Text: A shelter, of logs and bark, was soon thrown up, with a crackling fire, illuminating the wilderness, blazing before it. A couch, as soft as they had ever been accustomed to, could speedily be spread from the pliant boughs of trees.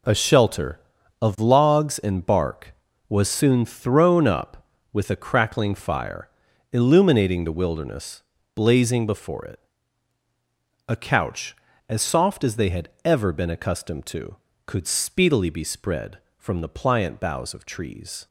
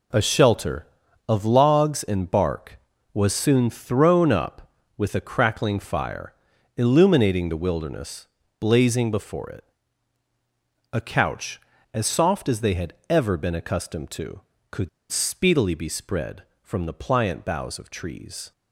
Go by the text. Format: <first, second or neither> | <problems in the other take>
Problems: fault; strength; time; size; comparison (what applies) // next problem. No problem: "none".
first | pauses between "had" and "ever"; slight; at 12.9 s; 0.18 s long; slight in the first // pauses between "could" and "speedily"; slight; at 14.8 s; 0.22 s long